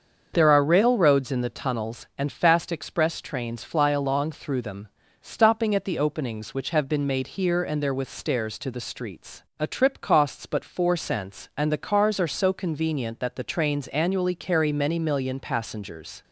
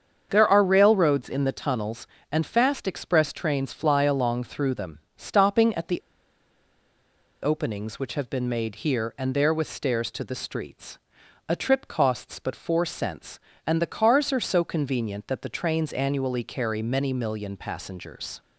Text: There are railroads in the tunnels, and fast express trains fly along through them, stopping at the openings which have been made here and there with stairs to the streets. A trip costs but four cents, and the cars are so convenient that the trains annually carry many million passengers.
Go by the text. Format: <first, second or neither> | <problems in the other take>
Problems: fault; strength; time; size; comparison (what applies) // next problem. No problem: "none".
first | starts louder than the rest; strong; until 1.3 s; 7 dB; also in the first // pauses between "the" and "openings"; strong; at 6.0 s; 1.4 s long